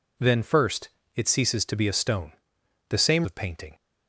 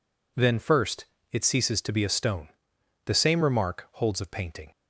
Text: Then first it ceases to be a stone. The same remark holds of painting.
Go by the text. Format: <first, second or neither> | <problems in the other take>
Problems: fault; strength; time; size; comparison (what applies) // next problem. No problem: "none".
second | pauses between "first" and "it"; slight; at 0.8 s; 0.26 s long; slight in the second // skips "remark holds"; at 3.2 s